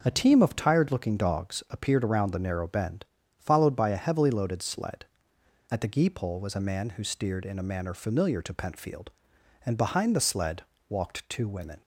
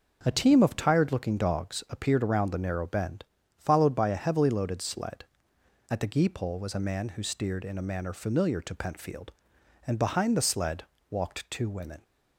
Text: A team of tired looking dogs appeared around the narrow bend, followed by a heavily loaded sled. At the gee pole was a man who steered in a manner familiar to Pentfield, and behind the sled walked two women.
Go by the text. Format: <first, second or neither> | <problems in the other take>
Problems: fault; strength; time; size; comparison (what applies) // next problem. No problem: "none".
neither | pauses between "sled" and "walked"; slight; the same in both